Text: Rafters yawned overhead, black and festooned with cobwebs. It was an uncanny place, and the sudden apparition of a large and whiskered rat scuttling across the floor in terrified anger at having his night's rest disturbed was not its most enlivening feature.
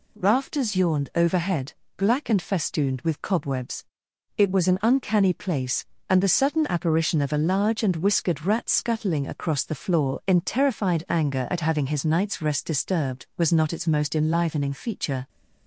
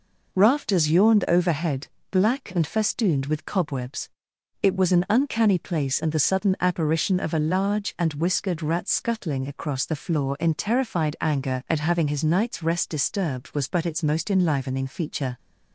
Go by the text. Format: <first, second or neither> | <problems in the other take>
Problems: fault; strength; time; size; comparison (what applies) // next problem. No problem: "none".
first | says "but" for "not"; at 13.6 s